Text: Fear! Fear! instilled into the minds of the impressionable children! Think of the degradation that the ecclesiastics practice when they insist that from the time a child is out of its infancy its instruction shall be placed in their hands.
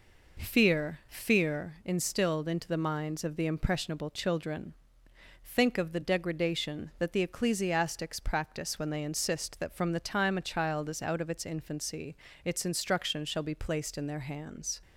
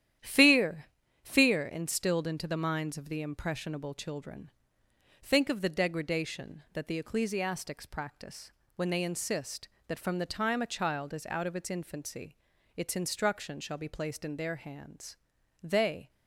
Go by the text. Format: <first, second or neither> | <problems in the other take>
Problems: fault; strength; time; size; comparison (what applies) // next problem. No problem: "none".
first | starts louder than the rest; strong; until 1.5 s; 11 dB // pauses between "practice" and "when"; slight; at 8.5 s; 0.24 s long // pauses between "infancy" and "its"; at 12.3 s; 0.40 s long; slight in the first // goes on to say "They"; slight; from 15.6 s on; 0.48 s long